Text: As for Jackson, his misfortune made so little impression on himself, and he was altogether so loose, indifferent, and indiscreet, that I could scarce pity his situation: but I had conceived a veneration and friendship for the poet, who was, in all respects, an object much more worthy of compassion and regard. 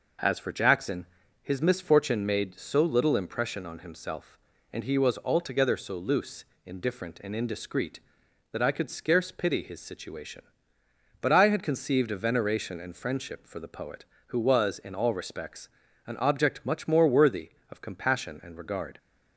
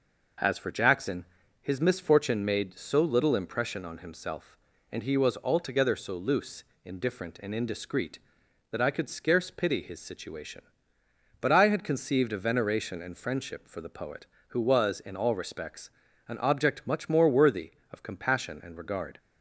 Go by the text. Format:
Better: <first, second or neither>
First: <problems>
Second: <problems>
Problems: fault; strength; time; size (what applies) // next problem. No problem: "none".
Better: neither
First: none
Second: none